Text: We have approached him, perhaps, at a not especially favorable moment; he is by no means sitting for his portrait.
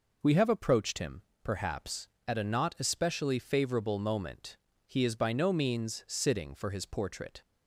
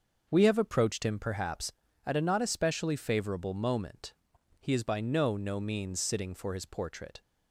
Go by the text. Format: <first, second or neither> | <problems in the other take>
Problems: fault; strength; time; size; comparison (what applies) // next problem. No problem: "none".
first | starts louder than the rest; noticeable; until 1.2 s; 6 dB // says "no" twice; at 5.3 s